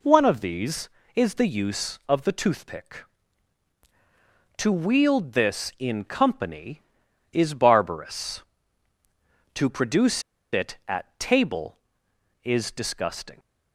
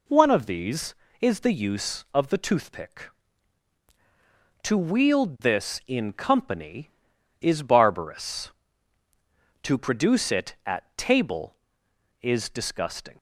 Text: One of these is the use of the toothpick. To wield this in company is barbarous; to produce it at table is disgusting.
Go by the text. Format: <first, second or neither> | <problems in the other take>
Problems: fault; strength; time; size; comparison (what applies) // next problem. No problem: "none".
second | pauses between "produce" and "it"; slight; at 10.2 s; 0.30 s long